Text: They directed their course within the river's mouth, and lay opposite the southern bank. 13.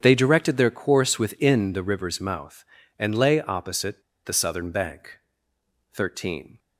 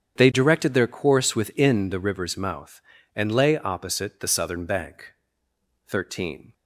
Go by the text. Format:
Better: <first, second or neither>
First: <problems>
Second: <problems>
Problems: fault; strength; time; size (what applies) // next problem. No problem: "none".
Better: second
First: starts louder than the rest; strong; until 1.0 s; 8 dB // pauses between "opposite" and "the"; slight; at 4.0 s; 0.23 s long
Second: starts louder than the rest; strong; until 1.2 s; 8.5 dB